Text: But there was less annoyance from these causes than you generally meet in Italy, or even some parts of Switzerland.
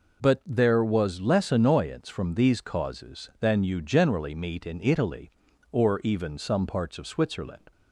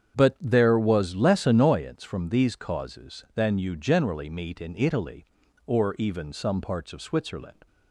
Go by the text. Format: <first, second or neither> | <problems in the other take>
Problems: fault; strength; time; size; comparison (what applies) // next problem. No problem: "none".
first | starts louder than the rest; strong; until 2.0 s; 8 dB